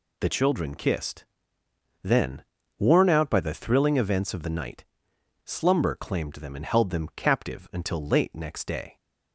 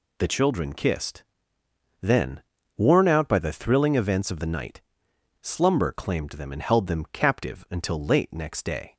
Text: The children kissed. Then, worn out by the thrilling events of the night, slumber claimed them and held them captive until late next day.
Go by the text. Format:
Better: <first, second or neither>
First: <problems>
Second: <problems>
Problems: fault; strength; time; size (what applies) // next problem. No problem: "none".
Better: neither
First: none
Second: none